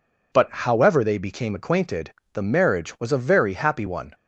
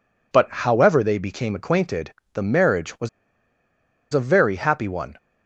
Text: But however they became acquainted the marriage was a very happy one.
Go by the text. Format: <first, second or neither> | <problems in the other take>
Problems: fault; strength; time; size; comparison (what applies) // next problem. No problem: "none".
first | pauses between "acquainted" and "the"; slight; at 2.1 s; 0.18 s long; slight in the first // pauses between "was" and "a"; at 3.0 s; 1.0 s long